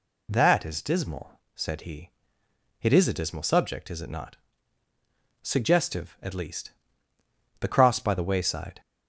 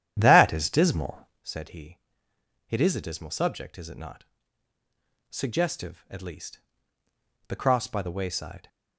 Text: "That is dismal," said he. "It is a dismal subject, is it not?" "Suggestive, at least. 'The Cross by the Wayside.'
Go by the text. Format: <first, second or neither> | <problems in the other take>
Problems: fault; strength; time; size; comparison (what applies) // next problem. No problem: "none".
first | starts louder than the rest; strong; until 1.5 s; 10.5 dB